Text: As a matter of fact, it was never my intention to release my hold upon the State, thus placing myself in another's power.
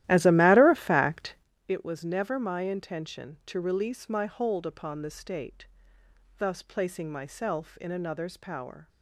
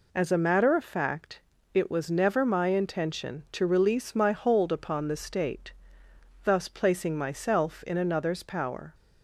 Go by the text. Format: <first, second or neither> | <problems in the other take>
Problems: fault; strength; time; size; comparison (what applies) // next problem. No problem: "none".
second | starts louder than the rest; strong; until 1.5 s; 14 dB